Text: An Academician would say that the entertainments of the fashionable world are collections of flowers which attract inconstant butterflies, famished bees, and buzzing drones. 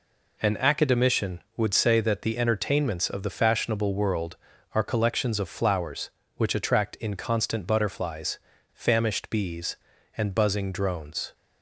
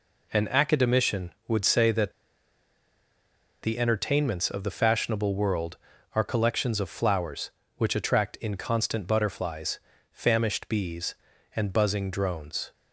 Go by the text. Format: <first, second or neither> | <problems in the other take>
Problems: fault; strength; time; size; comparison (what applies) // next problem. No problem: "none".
first | pauses between "that" and "the"; strong; at 2.1 s; 1.4 s long